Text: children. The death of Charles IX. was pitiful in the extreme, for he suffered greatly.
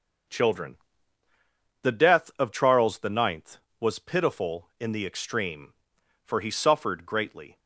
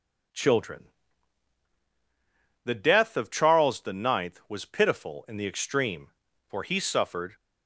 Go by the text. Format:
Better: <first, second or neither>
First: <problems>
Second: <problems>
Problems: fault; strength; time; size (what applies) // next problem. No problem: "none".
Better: first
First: none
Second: stops before "greatly"; at 7.3 s